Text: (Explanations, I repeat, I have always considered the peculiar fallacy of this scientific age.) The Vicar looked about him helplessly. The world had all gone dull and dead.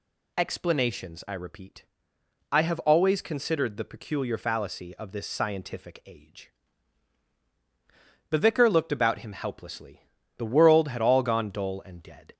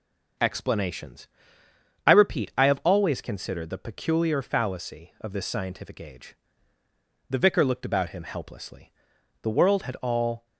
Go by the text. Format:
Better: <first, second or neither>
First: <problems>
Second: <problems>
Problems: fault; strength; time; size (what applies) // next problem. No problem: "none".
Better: first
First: none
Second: stops before "gone dull and dead"; at 10.4 s